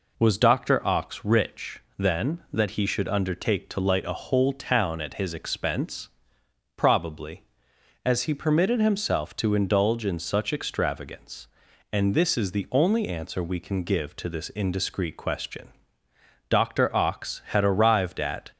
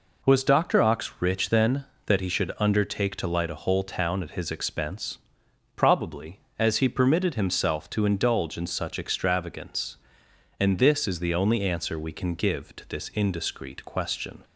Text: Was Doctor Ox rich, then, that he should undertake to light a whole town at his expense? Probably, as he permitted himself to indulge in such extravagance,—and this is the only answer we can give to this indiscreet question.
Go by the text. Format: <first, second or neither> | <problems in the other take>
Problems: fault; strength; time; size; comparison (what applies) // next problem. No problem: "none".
second | goes on to say "Doctor Ox had arrived at"; strong; from 16.4 s on; 2.0 s long